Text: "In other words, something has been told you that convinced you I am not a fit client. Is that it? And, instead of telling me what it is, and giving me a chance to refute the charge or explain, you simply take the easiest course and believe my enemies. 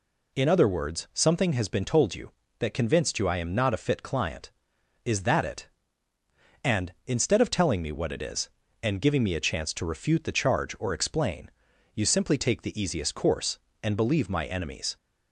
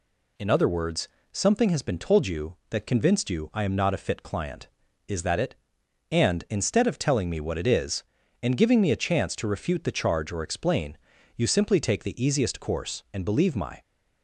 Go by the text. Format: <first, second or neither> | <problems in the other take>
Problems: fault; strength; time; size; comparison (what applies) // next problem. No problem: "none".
first | stops before "enemies"; at 13.8 s